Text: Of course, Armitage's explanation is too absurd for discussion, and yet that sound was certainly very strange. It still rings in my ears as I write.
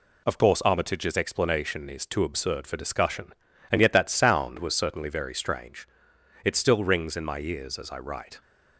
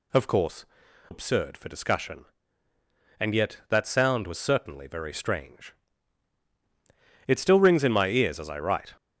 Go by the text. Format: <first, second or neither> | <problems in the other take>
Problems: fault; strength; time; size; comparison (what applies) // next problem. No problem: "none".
first | skips "Armitage's explanation is too"; at 0.8 s